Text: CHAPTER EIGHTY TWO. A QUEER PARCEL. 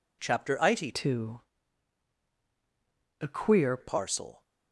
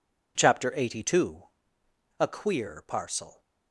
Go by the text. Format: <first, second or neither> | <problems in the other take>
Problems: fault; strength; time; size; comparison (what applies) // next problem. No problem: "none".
second | changes voice from "TWO" to "QUEER"; from 0.9 to 3.7 s; 2.8 s long